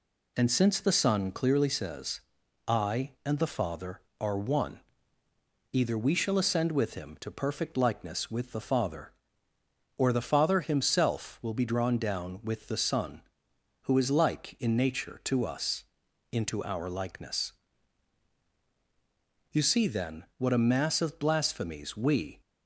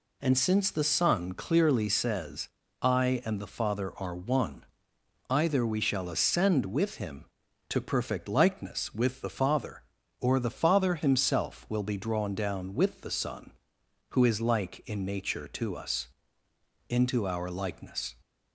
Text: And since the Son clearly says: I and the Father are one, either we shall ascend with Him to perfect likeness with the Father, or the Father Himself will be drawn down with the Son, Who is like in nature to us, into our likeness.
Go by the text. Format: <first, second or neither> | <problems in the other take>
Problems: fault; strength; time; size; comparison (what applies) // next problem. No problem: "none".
second | goes on to say "You see then what a mass of blasphemies we"; strong; from 19.5 s on; 2.9 s long